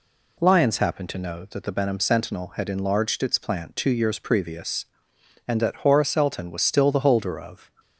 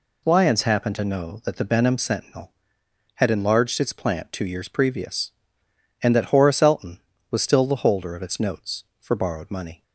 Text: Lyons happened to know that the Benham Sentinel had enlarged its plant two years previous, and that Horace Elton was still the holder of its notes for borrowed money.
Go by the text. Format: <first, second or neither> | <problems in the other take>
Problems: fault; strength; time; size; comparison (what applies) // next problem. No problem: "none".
second | stops before "its notes for borrowed money"; at 7.7 s